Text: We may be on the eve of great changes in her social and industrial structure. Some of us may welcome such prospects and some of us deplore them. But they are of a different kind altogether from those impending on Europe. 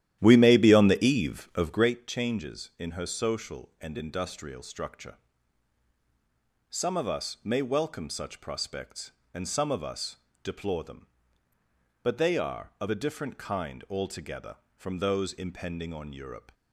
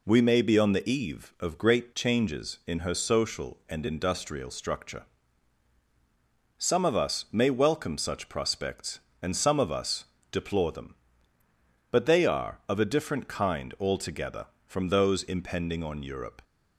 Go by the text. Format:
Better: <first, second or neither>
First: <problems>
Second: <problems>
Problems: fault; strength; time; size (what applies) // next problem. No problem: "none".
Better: second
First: starts louder than the rest; strong; until 2.0 s; 12 dB // pauses between "us" and "deplore"; slight; at 10.1 s; 0.28 s long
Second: pauses between "us" and "deplore"; slight; at 10.0 s; 0.28 s long